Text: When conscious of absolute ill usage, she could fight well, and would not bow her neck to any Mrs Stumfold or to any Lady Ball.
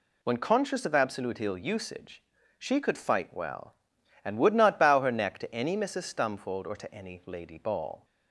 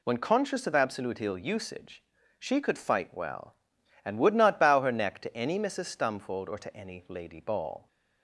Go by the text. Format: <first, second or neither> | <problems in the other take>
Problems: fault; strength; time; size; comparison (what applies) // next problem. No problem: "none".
neither | none